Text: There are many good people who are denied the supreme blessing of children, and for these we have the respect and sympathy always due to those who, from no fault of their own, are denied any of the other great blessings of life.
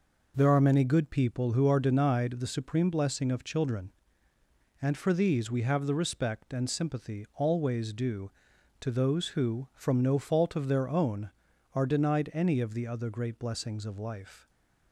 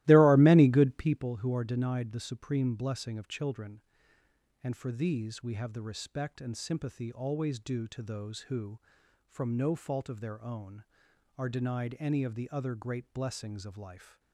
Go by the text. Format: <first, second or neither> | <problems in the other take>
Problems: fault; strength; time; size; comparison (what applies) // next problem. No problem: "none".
first | starts louder than the rest; strong; until 1.3 s; 17.5 dB